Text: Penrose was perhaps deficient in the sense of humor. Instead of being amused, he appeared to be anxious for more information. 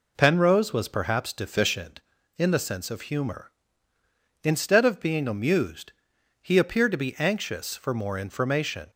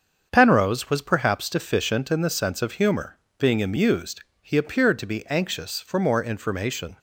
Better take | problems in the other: first | starts louder than the rest; strong; until 1.3 s; 7 dB // skips "Instead of"; at 3.2 s

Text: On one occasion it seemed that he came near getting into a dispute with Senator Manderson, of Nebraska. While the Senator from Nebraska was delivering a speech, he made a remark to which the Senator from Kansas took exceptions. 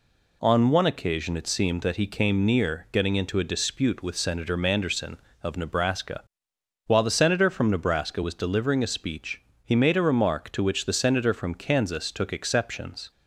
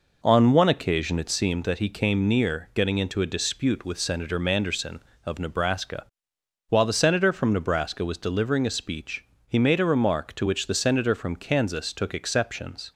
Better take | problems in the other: first | starts louder than the rest; noticeable; until 1.4 s; 5 dB

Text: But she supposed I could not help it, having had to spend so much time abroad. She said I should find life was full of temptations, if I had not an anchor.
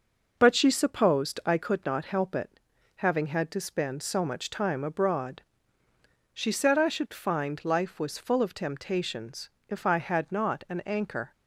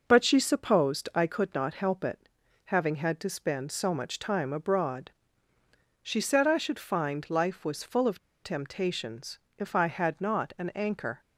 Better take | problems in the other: first | pauses between "of" and "temptations"; slight; at 8.1 s; 0.25 s long

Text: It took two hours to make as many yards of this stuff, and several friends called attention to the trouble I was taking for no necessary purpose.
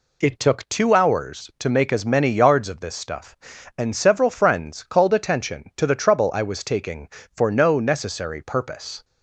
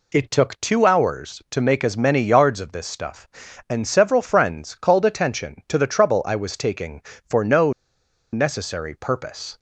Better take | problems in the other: first | pauses between "no" and "necessary"; noticeable; at 7.7 s; 0.59 s long

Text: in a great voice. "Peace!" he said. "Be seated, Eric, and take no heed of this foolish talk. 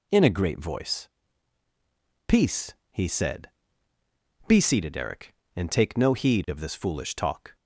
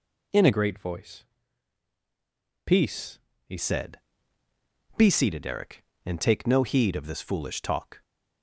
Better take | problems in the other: first | changes voice from "great" to "he"; from 0.5 to 3.5 s; 3.0 s long

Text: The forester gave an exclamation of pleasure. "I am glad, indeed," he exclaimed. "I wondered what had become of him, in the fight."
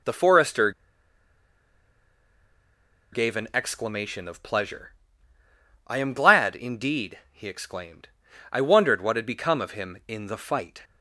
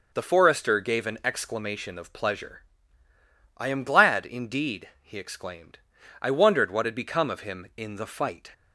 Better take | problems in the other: second | pauses between "forester" and "gave"; strong; at 0.7 s; 2.4 s long

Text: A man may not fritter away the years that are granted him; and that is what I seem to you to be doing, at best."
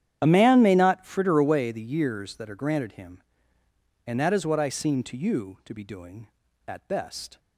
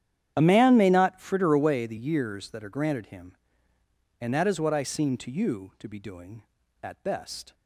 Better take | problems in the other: neither | starts louder than the rest; strong; the same in both

